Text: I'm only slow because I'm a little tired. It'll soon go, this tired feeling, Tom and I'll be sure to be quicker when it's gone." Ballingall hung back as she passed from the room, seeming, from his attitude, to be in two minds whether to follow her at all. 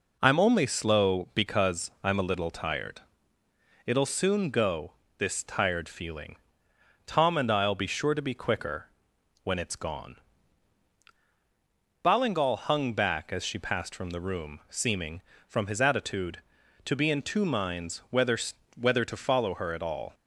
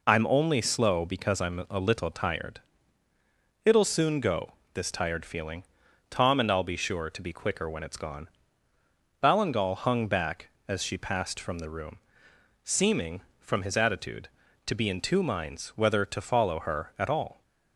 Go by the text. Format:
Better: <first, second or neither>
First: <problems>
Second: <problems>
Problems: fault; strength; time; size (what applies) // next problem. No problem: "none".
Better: second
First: pauses between "quicker" and "when"; noticeable; at 8.8 s; 0.56 s long // says "whether" twice; at 18.7 s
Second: none